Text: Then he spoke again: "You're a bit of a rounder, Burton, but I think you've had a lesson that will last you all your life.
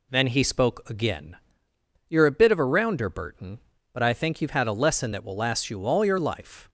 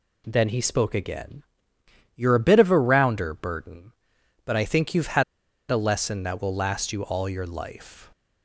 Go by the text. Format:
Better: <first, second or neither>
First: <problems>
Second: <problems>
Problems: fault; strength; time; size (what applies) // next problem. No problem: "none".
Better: first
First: none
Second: pauses between "had" and "a"; noticeable; at 5.2 s; 0.47 s long